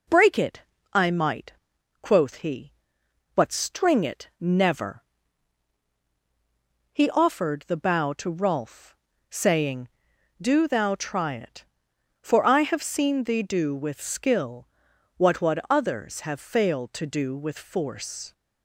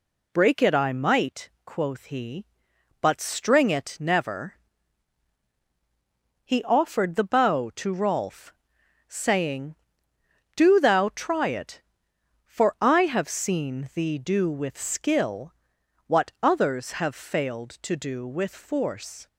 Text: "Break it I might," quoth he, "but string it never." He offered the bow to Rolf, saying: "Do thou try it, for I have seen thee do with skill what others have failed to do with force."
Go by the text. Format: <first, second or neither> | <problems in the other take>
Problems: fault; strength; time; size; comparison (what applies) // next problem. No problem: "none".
second | pauses between "it" and "I"; slight; at 0.6 s; 0.32 s long // pauses between "skill" and "what"; noticeable; at 14.6 s; 0.52 s long; noticeable in the second // says "what" twice; at 15.4 s